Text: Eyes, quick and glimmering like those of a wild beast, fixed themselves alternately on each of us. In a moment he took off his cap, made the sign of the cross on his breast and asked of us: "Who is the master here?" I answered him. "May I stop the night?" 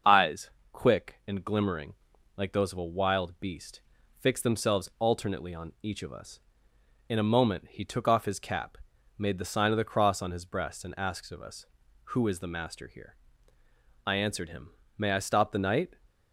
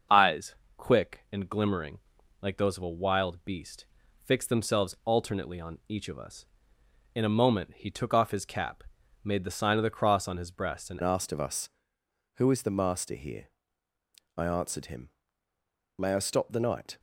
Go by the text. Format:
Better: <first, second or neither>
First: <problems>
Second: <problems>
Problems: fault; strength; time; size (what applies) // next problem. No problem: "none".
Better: first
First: starts louder than the rest; until 1.4 s; 6.5 dB // pauses between "glimmering" and "like"; at 1.9 s; 0.42 s long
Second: starts louder than the rest; until 1.4 s; 6.5 dB // pauses between "glimmering" and "like"; at 1.9 s; 0.42 s long // changes voice at "asked"; from 11.0 s on; 5.9 s long